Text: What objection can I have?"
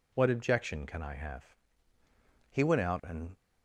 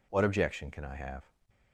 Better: second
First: goes on to say "He went out and"; noticeable; from 2.5 s on; 0.83 s long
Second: none

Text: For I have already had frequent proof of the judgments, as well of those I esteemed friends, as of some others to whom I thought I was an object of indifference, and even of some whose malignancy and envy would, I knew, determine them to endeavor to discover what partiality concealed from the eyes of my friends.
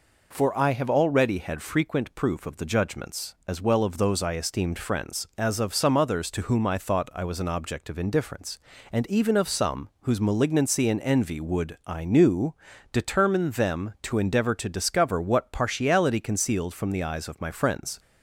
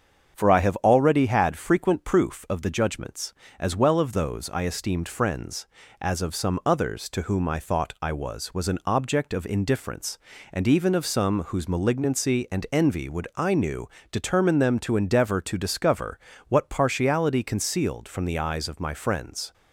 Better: first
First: none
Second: starts louder than the rest; until 1.3 s; 7 dB // says "was" twice; at 8.5 s // pauses between "discover" and "what"; slight; at 16.1 s; 0.30 s long

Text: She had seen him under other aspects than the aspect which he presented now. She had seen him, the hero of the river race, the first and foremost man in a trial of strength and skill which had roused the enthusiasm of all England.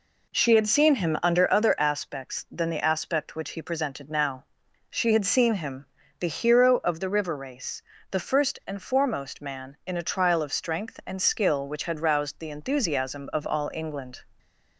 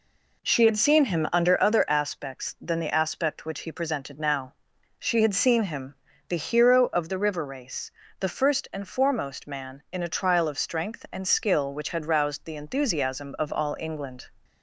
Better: neither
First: none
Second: none

